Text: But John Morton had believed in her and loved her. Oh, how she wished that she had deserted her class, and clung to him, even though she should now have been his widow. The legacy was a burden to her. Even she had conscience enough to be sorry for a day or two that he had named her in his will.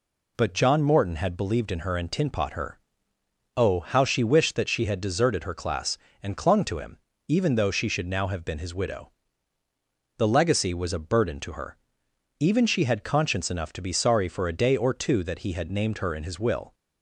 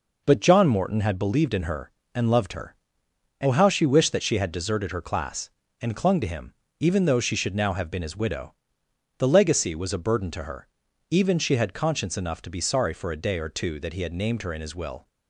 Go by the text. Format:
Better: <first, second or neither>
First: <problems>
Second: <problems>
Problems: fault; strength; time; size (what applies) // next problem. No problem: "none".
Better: second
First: says "tinpot" for "loved"; at 2.1 s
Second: none